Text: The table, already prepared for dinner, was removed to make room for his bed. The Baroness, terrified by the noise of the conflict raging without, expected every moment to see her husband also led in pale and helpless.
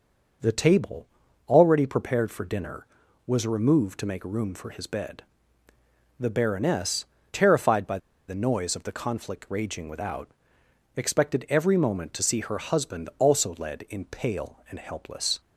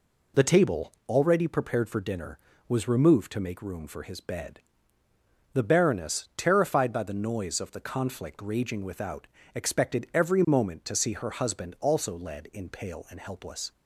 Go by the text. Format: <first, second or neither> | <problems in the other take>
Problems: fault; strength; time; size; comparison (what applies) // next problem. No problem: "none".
second | starts louder than the rest; noticeable; until 1.8 s; 6 dB // pauses between "by" and "the"; slight; at 7.9 s; 0.30 s long